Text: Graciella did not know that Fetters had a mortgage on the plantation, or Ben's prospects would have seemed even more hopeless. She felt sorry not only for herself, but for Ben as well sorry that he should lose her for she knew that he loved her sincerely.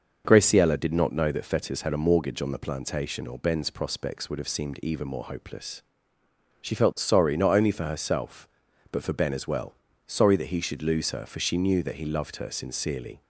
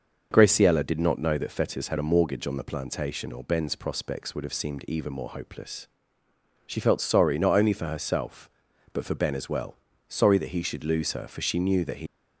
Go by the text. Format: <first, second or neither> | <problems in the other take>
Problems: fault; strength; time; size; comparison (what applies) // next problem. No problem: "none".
first | starts louder than the rest; noticeable; until 1.3 s; 6 dB; noticeable in the first // pauses between "well" and "sorry"; at 9.7 s; 0.38 s long; also in the first // stops before "loved her sincerely"; at 12.0 s